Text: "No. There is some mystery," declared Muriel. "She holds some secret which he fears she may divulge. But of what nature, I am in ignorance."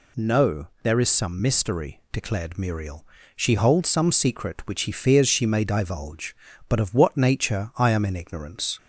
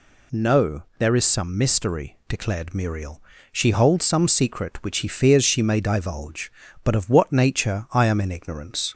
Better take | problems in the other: neither | none

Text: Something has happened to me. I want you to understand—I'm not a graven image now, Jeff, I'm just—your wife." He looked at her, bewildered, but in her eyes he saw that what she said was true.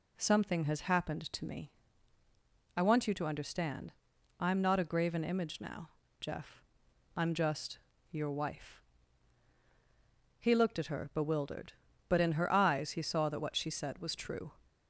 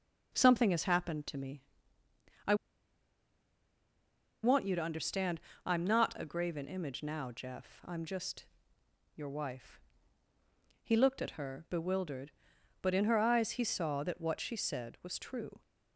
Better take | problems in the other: first | pauses between "I" and "want"; strong; at 2.5 s; 1.8 s long

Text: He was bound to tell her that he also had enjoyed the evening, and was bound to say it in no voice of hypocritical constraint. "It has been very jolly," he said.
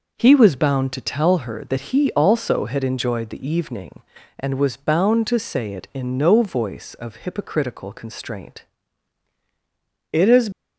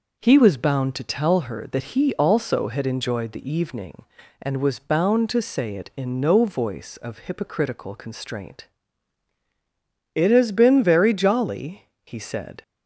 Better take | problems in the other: second | stops before "been very jolly he said"; at 10.5 s

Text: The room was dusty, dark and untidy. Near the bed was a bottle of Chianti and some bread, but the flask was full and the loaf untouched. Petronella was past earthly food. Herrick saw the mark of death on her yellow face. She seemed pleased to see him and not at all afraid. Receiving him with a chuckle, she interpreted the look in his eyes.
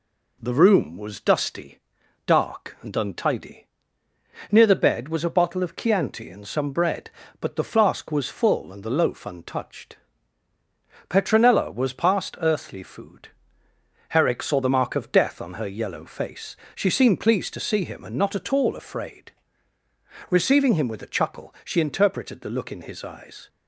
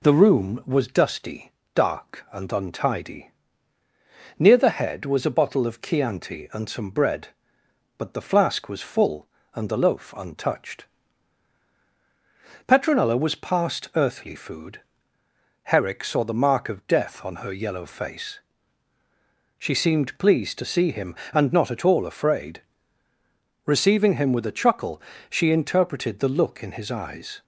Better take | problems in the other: first | says "head" for "bed"; at 4.7 s

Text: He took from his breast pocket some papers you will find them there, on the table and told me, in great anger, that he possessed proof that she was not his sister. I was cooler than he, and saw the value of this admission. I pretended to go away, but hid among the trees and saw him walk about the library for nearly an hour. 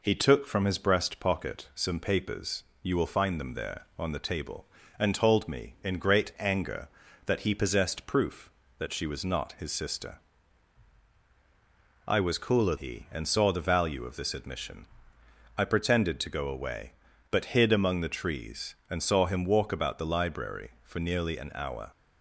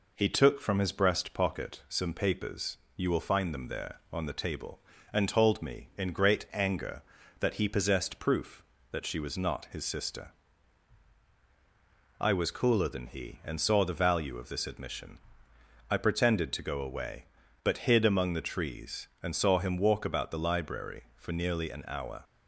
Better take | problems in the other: second | pauses between "papers" and "you"; slight; at 2.6 s; 0.20 s long; slight in the second // skips "than"; at 12.7 s

